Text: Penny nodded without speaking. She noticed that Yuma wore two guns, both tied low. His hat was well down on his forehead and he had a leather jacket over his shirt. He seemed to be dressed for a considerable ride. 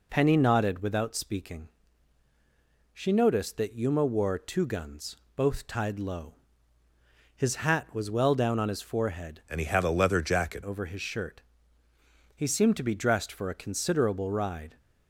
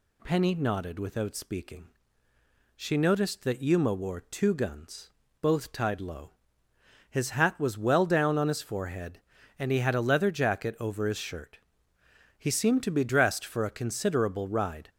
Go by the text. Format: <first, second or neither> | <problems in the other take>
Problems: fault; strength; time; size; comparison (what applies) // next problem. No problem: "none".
second | changes voice from "and" to "jacket"; from 9.4 to 10.6 s; 1.2 s long